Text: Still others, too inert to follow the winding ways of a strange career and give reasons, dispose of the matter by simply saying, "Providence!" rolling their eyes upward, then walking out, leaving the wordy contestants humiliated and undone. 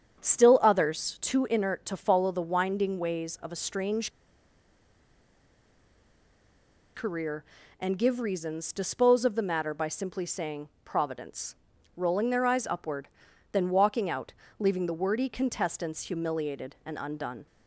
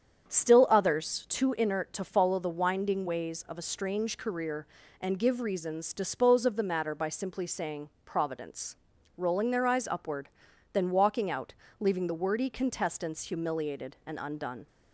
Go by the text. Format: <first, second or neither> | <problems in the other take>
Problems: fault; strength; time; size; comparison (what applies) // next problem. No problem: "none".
second | starts louder than the rest; strong; until 1.2 s; 8 dB; strong in the second // pauses between "strange" and "career"; strong; at 4.0 s; 2.8 s long